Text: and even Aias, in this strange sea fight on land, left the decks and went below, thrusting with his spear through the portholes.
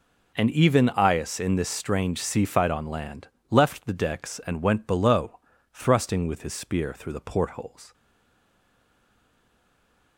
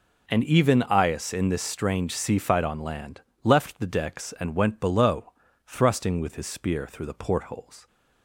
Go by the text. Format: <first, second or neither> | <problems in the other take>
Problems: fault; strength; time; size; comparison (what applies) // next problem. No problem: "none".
second | stays silent after the last word; from 7.9 s on; 2.2 s long